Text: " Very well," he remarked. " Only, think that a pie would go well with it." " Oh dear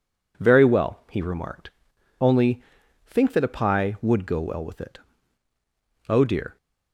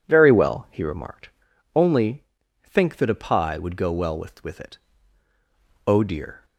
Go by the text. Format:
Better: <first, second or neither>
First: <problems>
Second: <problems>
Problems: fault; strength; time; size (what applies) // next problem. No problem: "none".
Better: first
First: none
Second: starts louder than the rest; strong; until 1.0 s; 10 dB // says "with" twice; at 4.4 s